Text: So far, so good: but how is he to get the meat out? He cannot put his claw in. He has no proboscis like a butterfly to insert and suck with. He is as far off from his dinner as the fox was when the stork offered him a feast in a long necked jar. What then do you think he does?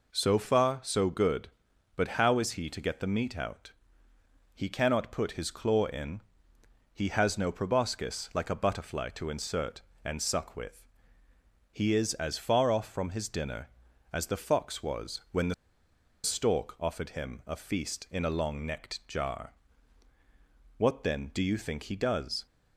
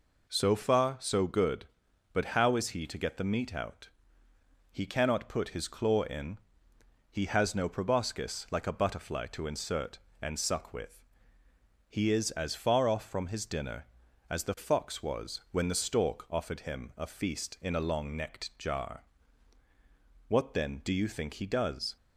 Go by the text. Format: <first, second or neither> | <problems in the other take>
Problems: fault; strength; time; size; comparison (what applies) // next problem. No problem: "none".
second | pauses between "the" and "stork"; noticeable; at 15.5 s; 0.69 s long